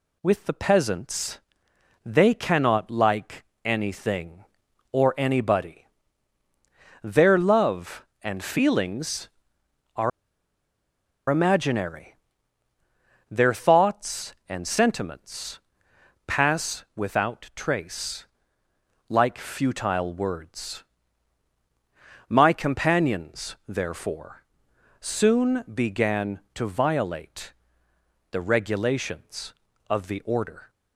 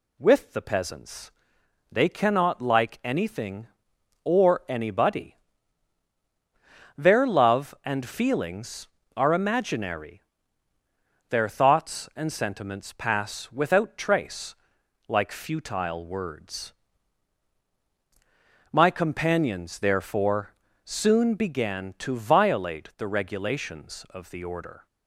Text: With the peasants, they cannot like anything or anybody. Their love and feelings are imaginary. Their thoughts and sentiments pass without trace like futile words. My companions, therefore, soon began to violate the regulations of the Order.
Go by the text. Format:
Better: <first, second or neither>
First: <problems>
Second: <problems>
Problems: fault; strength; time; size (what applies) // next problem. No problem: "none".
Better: second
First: pauses between "like" and "anything"; slight; at 3.4 s; 0.20 s long // pauses between "are" and "imaginary"; at 10.1 s; 1.1 s long // pauses between "sentiments" and "pass"; noticeable; at 15.5 s; 0.66 s long // pauses between "trace" and "like"; noticeable; at 18.2 s; 0.86 s long // pauses between "violate" and "the"; noticeable; at 27.5 s; 0.80 s long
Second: pauses between "trace" and "like"; noticeable; at 14.5 s; 0.54 s long